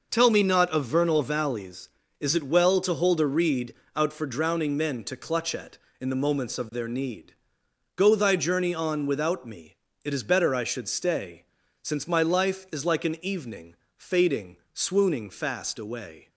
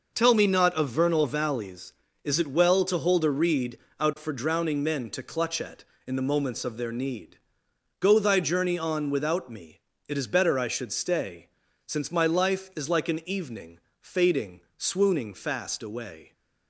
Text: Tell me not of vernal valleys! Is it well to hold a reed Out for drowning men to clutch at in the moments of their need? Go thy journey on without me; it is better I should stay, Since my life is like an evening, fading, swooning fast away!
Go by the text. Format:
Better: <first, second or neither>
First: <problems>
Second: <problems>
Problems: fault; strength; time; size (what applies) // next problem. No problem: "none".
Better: neither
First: pauses between "reed" and "Out"; slight; at 3.7 s; 0.20 s long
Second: pauses between "reed" and "Out"; slight; at 3.7 s; 0.20 s long